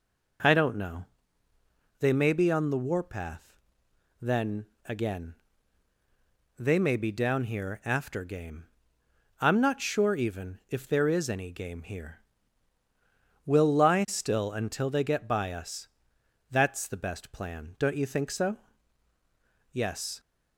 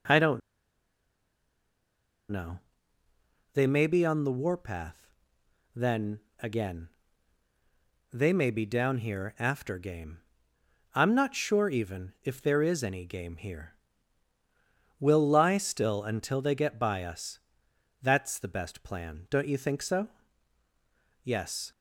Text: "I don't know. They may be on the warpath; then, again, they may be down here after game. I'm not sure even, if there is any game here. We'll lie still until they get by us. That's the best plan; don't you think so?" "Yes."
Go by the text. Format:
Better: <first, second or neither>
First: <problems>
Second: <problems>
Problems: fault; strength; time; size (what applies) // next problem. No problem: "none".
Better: first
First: none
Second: pauses between "don't" and "know"; strong; at 0.4 s; 1.8 s long